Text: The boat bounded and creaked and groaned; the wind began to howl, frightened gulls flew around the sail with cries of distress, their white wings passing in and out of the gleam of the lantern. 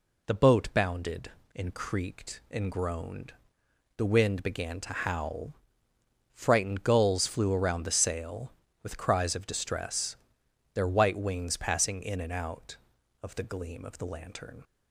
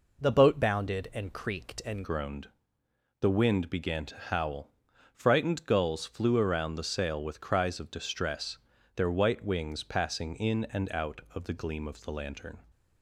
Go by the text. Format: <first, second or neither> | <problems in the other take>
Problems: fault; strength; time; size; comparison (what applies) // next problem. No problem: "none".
first | changes voice at "groaned"; from 2.0 s on; 10.6 s long